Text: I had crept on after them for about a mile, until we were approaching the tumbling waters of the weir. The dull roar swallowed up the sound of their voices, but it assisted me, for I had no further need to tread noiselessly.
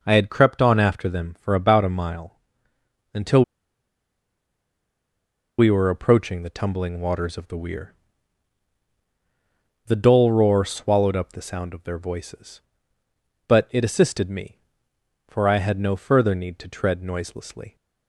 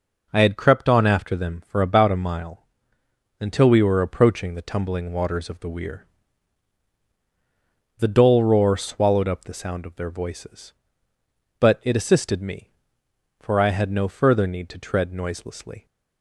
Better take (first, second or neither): second